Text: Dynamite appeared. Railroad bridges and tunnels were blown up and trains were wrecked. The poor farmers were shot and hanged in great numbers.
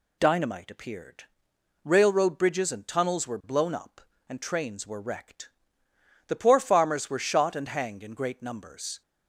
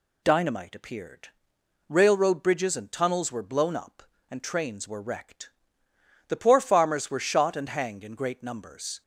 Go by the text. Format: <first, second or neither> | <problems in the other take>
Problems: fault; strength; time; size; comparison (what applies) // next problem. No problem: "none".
neither | none